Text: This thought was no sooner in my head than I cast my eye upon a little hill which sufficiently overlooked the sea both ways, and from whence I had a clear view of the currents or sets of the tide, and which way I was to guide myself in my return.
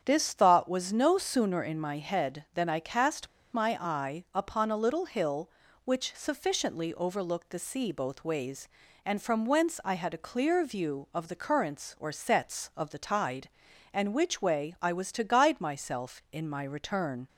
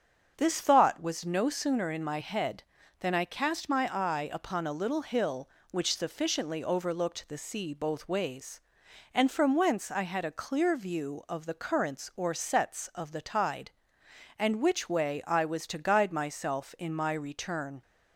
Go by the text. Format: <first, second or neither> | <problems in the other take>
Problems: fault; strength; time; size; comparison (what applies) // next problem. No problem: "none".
second | starts louder than the rest; strong; until 1.0 s; 8 dB; strong in the second // pauses between "cast" and "my"; slight; at 3.2 s; 0.25 s long